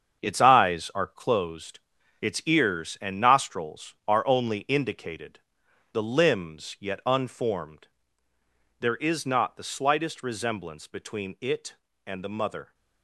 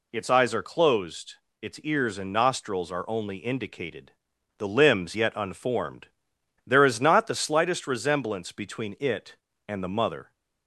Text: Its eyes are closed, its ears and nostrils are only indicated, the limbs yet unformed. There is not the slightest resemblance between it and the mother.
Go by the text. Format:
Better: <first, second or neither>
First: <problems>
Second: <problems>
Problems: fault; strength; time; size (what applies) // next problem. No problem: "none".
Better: second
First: gets quieter; strong; throughout; 9 dB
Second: none